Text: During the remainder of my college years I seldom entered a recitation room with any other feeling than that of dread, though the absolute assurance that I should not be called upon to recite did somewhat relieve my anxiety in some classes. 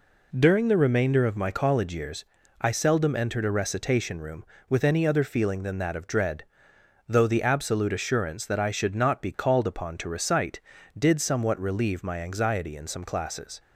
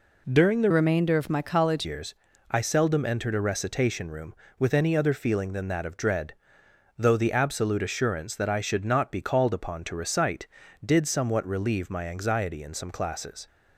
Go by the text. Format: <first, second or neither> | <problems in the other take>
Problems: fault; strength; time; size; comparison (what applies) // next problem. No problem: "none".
first | changes voice from "remainder" to "college"; from 0.7 to 1.8 s; 1.1 s long // pauses between "years" and "I"; slight; at 2.1 s; 0.34 s long; slight in the first